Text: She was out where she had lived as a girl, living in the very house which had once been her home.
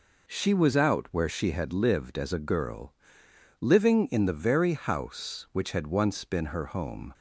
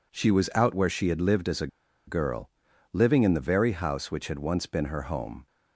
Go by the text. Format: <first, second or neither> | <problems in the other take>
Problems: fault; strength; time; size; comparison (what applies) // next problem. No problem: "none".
first | pauses between "a" and "girl"; at 1.6 s; 0.40 s long